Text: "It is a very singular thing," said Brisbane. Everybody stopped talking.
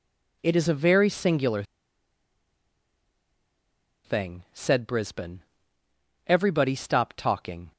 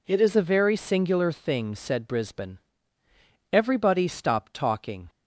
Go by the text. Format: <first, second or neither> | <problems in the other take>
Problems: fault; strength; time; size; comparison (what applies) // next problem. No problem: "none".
second | pauses between "singular" and "thing"; strong; at 1.6 s; 2.4 s long